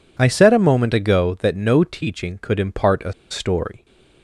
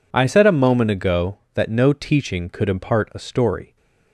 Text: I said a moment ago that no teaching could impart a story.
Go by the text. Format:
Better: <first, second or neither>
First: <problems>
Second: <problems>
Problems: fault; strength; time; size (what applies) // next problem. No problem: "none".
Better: second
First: pauses between "a" and "story"; slight; at 3.1 s; 0.18 s long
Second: none